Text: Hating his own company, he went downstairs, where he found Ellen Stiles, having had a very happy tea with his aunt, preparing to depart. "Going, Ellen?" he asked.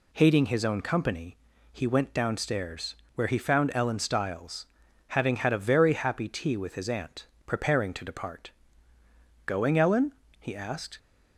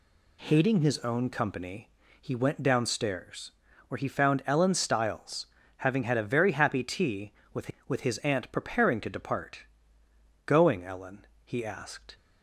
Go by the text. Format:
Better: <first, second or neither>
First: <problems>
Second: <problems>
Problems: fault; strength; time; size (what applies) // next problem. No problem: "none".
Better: first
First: none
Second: says "with" twice; at 7.8 s